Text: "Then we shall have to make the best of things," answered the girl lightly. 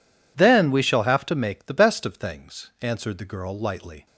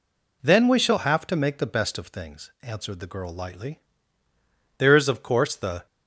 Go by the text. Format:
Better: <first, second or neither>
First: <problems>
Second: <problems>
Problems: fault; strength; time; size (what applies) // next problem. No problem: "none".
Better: first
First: none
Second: goes on to say "There is of course the"; noticeable; from 4.7 s on; 1.0 s long